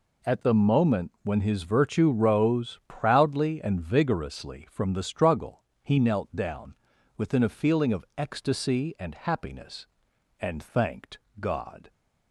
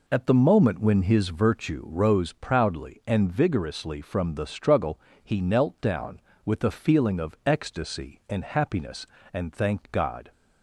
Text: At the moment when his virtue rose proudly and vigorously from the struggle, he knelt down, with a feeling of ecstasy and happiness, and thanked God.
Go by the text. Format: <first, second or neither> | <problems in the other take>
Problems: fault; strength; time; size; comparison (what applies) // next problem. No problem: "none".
second | says "within" for "with"; at 7.1 s // pauses between "thanked" and "God"; slight; at 11.1 s; 0.22 s long